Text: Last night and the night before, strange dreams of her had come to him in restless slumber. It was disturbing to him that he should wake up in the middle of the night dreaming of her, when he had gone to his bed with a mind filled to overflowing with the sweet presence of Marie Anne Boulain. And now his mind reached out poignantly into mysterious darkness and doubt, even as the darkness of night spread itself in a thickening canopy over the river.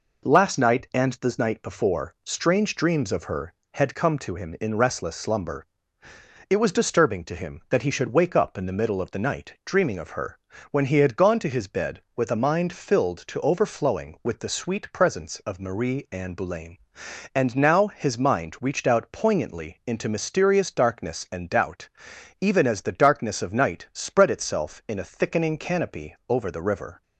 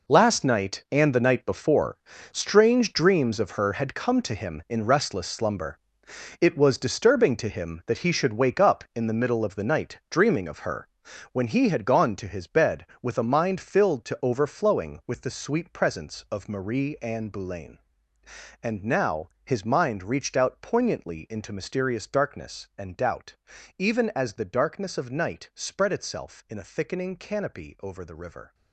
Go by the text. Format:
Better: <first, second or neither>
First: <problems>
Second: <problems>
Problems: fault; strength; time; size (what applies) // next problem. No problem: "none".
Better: first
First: none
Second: gets quieter; strong; throughout; 12 dB // pauses between "now" and "his"; slight; at 19.2 s; 0.18 s long